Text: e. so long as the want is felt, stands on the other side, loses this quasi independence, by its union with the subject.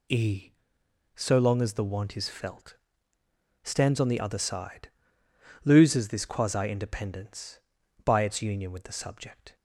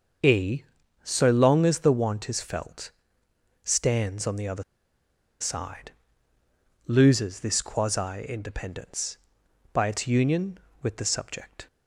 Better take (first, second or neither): first